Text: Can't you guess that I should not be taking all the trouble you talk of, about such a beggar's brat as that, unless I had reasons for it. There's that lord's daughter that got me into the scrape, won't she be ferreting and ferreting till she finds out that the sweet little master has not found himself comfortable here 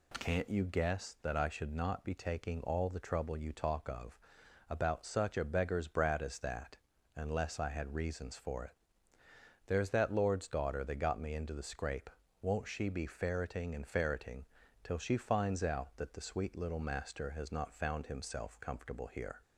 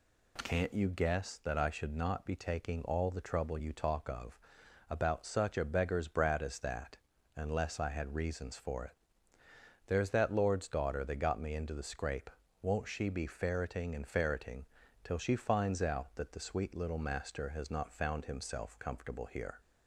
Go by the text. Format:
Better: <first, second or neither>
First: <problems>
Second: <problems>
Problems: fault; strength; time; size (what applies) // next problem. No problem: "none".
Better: neither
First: pauses between "ferreting" and "till"; at 14.4 s; 0.38 s long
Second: pauses between "ferreting" and "till"; at 14.6 s; 0.38 s long